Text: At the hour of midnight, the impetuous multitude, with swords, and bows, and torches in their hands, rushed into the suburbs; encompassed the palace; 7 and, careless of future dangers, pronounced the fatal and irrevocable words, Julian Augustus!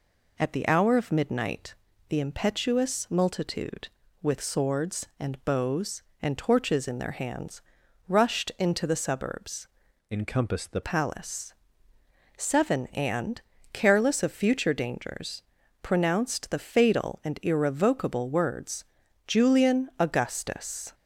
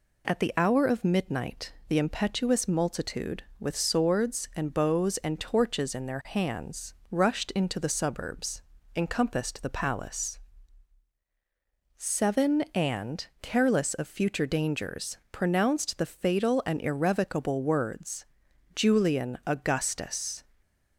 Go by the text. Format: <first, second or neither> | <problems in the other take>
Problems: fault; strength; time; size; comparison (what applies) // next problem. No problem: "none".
second | changes voice from "encompassed" to "the"; from 10.1 to 10.8 s; 0.7 s long